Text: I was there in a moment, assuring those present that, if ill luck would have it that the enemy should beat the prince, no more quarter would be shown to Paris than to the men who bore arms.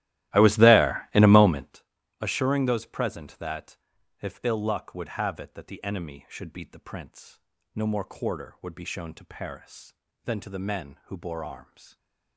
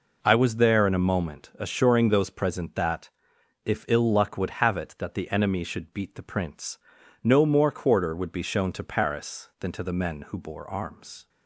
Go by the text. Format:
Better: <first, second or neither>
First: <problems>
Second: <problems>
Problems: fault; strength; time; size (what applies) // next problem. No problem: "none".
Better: second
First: starts louder than the rest; strong; until 1.8 s; 15.5 dB // stays silent after the last word; slight; from 11.8 s on; 0.5 s long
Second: none